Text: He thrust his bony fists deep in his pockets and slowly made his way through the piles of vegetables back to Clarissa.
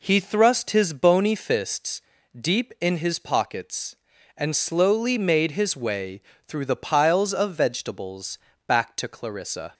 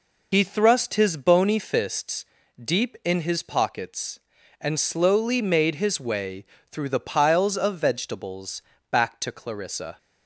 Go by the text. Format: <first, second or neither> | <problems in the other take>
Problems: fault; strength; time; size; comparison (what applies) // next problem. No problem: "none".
first | loses the start of "He"; at 0.3 s; 60 ms // pauses between "fists" and "deep"; slight; at 2.2 s; 0.34 s long; slight in the first // pauses between "way" and "through"; slight; at 6.4 s; 0.26 s long; slight in the first // pauses between "vegetables" and "back"; slight; at 8.6 s; 0.26 s long; slight in the first